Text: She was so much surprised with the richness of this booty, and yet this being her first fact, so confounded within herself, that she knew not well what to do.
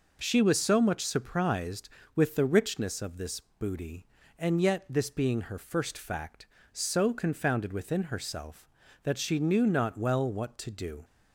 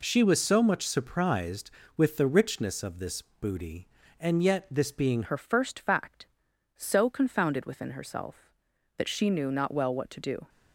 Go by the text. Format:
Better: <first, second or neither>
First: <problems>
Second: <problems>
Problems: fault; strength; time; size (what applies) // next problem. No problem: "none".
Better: first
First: none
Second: changes voice at "her"; from 5.2 s on; 5.2 s long